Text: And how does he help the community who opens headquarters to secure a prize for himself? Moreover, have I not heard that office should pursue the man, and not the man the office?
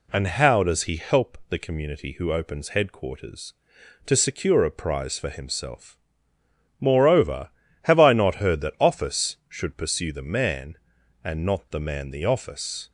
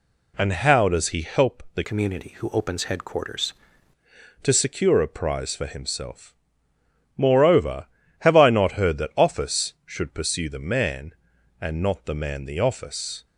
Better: first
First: none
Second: changes voice from "community" to "headquarters"; from 1.8 to 3.5 s; 1.7 s long

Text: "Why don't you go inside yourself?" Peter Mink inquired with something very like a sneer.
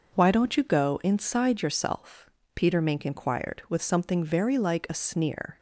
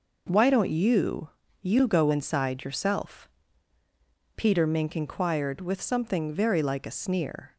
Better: first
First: none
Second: says "you" twice; at 1.6 s

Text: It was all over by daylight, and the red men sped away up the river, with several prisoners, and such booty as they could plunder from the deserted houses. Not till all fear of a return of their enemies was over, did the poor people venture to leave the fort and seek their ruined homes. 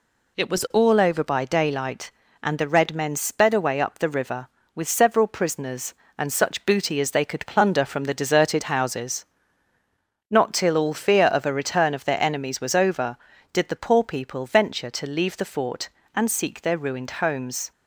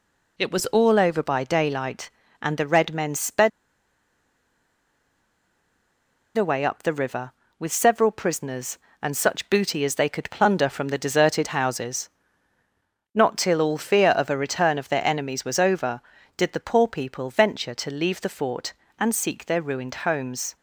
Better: first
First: none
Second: pauses between "sped" and "away"; strong; at 3.4 s; 2.8 s long

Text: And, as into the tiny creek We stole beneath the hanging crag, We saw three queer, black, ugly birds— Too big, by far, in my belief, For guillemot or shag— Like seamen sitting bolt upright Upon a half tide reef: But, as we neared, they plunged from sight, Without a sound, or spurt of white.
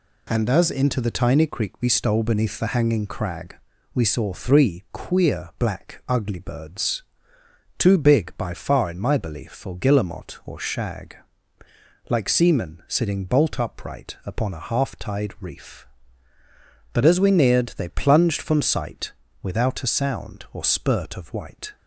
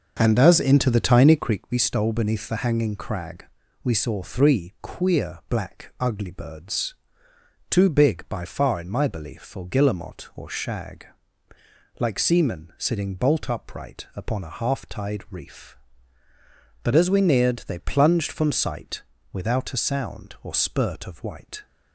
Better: first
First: none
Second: starts louder than the rest; until 1.6 s; 6 dB

